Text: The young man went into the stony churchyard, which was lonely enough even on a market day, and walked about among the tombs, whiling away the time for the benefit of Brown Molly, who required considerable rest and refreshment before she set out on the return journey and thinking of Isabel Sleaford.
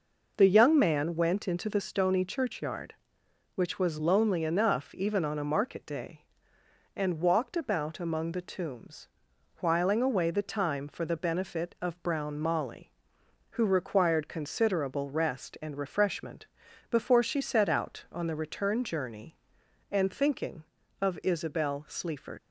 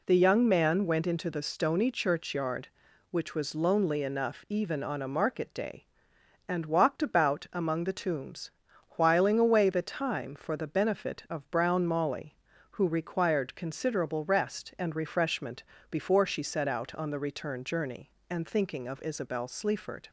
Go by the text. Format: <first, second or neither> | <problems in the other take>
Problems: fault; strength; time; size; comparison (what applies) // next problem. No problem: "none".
second | pauses between "refreshment" and "before"; at 16.4 s; 0.44 s long; slight in the second // leaves "Sleaford" unfinished; at 22.3 s; 90 ms